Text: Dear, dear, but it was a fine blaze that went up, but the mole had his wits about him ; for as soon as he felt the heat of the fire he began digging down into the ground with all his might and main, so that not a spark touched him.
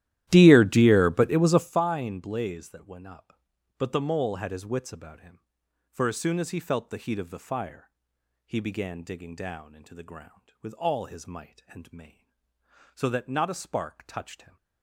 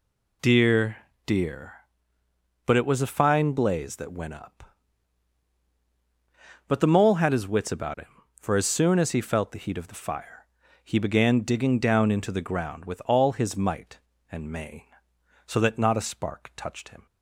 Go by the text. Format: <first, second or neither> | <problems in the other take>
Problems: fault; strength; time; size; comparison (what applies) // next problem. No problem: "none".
second | starts louder than the rest; strong; until 1.8 s; 13.5 dB // pauses between "fire" and "he"; noticeable; at 7.8 s; 0.54 s long; slight in the second